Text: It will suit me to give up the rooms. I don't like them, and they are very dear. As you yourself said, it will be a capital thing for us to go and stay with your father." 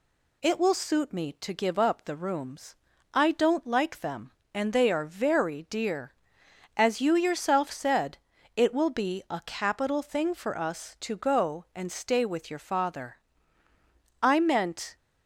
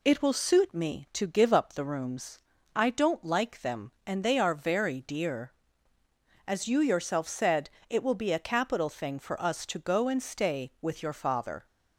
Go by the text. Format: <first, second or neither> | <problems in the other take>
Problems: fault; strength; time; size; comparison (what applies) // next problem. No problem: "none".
second | goes on to say "I meant"; noticeable; from 14.2 s on; 0.74 s long